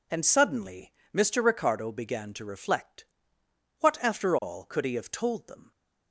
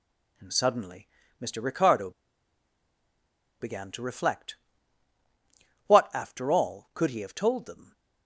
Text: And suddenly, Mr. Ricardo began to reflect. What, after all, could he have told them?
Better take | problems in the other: first | pauses between "Ricardo" and "began"; strong; at 2.0 s; 1.5 s long

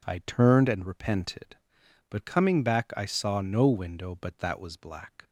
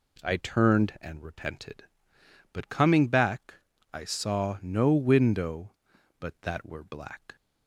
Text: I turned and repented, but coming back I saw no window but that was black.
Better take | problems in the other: first | pauses between "back" and "I"; at 3.5 s; 0.40 s long // says "were" for "was"; at 6.6 s

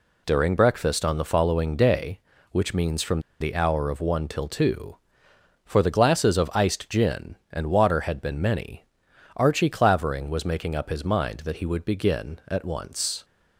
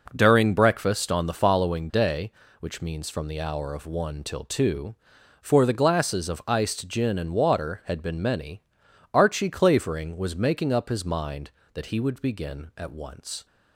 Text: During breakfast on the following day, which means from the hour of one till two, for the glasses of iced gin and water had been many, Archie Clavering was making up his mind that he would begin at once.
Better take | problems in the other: second | pauses between "from" and "the"; slight; at 3.1 s; 0.20 s long

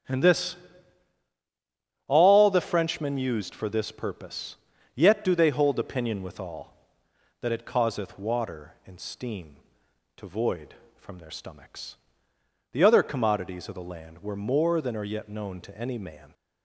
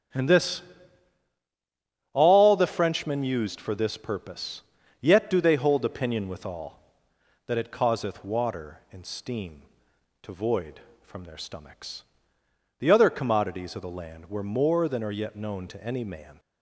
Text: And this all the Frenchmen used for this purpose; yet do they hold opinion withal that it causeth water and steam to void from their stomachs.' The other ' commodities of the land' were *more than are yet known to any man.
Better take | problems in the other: neither | starts louder than the rest; strong; the same in both // pauses between "this" and "all"; strong; the same in both

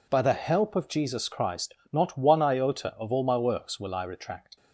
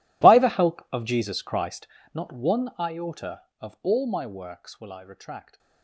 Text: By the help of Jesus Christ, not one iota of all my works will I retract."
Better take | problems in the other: first | gets quieter; strong; throughout; 18 dB

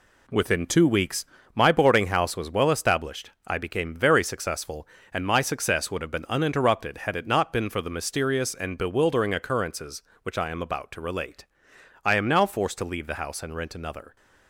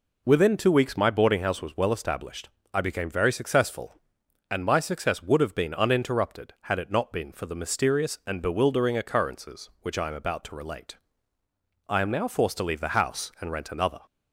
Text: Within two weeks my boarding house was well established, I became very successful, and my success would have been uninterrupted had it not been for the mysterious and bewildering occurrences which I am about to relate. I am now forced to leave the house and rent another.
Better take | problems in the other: second | gets quieter; strong; throughout; 7.5 dB // pauses between "weeks" and "my"; slight; at 1.2 s; 0.30 s long

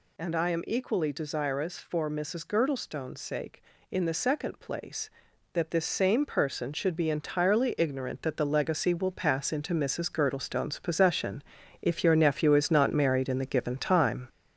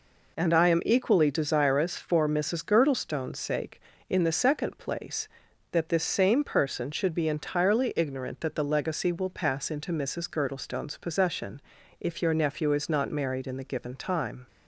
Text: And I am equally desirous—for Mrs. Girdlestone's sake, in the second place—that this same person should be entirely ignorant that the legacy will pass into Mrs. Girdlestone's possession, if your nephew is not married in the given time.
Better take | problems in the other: second | gets louder; noticeable; throughout; 4.5 dB

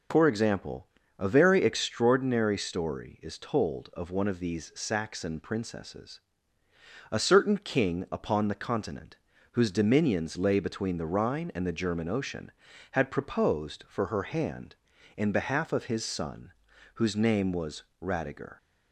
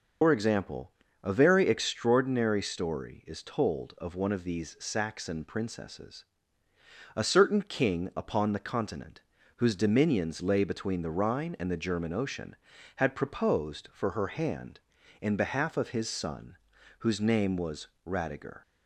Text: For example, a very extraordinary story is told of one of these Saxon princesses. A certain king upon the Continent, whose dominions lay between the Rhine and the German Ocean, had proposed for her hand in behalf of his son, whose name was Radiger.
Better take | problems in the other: first | loses the start of "For"; at 0.2 s; 70 ms // pauses between "was" and "Radiger"; slight; at 17.8 s; 0.18 s long; slight in the first

